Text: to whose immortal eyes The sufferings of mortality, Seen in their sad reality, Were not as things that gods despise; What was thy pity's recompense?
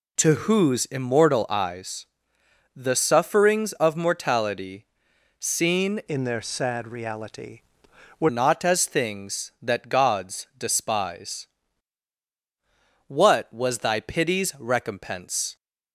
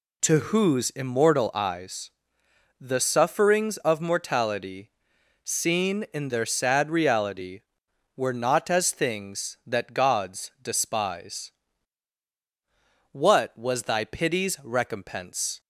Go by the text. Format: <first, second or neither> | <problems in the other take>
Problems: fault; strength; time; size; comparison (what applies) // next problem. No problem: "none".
second | pauses between "eyes" and "The"; noticeable; at 2.0 s; 0.70 s long; noticeable in the second // changes voice from "in" to "Were"; from 6.0 to 8.2 s; 2.2 s long